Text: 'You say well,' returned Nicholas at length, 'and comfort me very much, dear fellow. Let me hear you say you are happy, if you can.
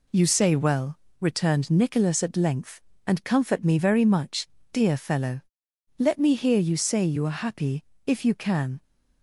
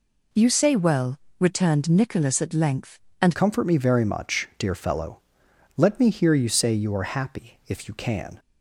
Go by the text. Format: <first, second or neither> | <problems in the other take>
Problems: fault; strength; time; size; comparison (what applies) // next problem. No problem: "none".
first | changes voice at "comfort"; from 3.3 s on; 5.0 s long